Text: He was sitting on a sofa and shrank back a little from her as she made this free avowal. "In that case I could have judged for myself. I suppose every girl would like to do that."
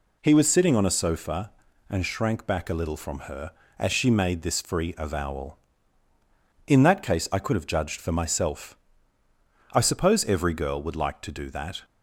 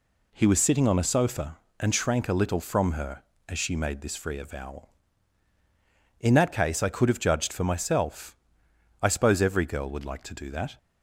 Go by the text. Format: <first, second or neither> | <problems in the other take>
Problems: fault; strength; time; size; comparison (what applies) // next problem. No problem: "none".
first | skips "back"; at 2.2 s